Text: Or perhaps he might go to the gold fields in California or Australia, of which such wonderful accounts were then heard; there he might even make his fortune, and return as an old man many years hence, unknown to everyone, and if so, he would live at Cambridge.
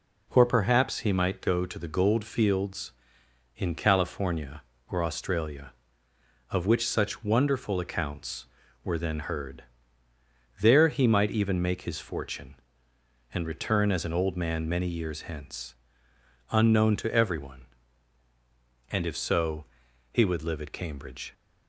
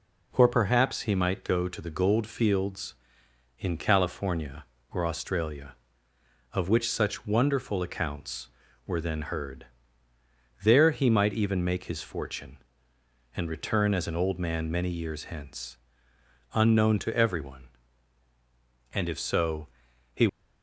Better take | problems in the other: first | stops before "would live at Cambridge"; at 20.2 s

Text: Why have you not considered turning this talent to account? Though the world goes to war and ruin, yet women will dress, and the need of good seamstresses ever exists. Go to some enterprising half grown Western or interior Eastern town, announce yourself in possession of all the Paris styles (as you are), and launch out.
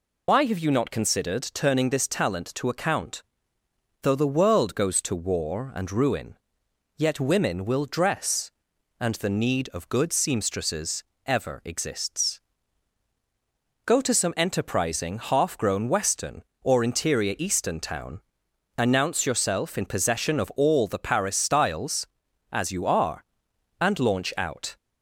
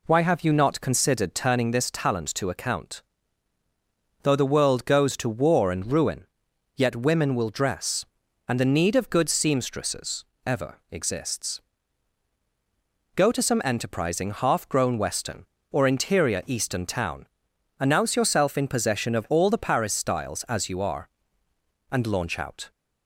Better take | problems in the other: second | loses the start of "Why"; at 0.2 s; 90 ms // pauses between "seamstresses" and "ever"; slight; at 11.0 s; 0.24 s long; slight in the second

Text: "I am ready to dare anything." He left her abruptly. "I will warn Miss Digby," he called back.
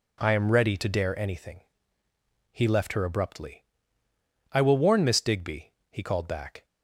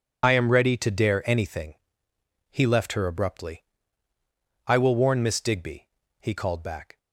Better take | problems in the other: first | loses the start of "I"; at 0.2 s; 40 ms

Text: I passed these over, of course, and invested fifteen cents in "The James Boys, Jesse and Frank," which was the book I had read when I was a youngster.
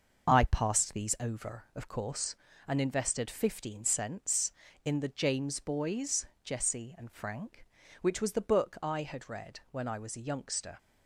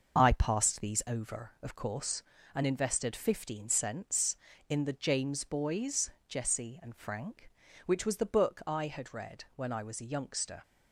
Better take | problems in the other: neither | starts louder than the rest; the same in both

